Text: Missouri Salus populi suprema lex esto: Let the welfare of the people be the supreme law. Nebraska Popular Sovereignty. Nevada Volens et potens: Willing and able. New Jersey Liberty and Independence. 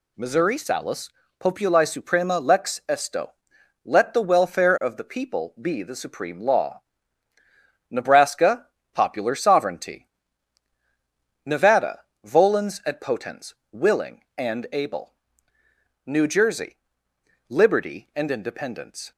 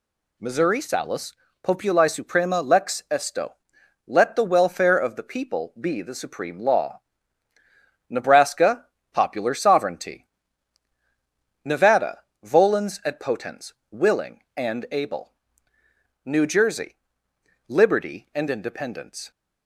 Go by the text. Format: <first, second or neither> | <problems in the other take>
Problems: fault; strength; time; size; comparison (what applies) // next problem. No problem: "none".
neither | pauses between "Salus" and "populi"; slight; the same in both // pauses between "Nebraska" and "Popular"; slight; the same in both // pauses between "Nevada" and "Volens"; slight; the same in both // pauses between "Jersey" and "Liberty"; noticeable; the same in both